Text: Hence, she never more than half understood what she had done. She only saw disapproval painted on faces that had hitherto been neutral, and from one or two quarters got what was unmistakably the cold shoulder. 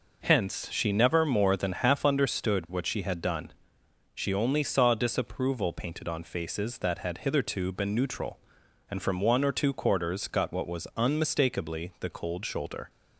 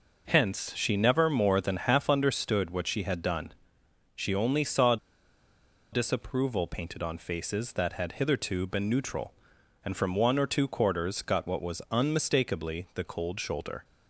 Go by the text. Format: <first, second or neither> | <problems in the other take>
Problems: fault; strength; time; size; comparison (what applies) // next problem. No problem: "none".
first | pauses between "saw" and "disapproval"; noticeable; at 4.9 s; 0.96 s long